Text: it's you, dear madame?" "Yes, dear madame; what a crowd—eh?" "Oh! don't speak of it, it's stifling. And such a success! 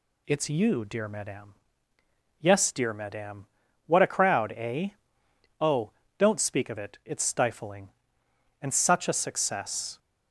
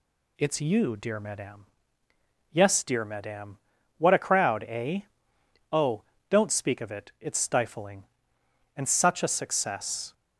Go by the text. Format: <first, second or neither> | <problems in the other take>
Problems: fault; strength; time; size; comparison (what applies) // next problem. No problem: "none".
neither | none